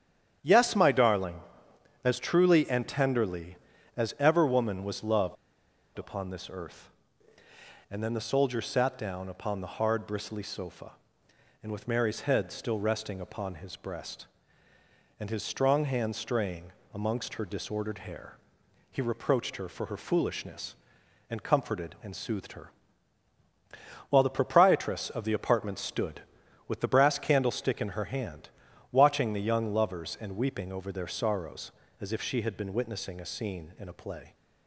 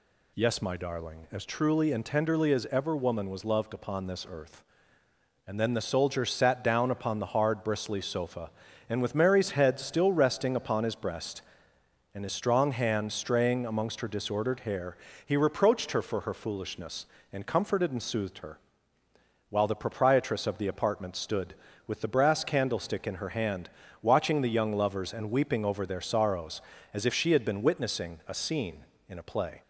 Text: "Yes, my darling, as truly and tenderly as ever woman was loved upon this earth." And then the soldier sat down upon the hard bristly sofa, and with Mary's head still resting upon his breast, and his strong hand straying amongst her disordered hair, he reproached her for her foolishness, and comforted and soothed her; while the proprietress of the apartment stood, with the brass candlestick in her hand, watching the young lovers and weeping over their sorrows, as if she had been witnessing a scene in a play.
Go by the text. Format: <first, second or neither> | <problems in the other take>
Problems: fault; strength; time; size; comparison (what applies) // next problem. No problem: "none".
second | starts louder than the rest; strong; until 1.4 s; 9 dB // pauses between "loved" and "upon"; noticeable; at 5.3 s; 0.61 s long // pauses between "straying" and "amongst"; slight; at 16.7 s; 0.20 s long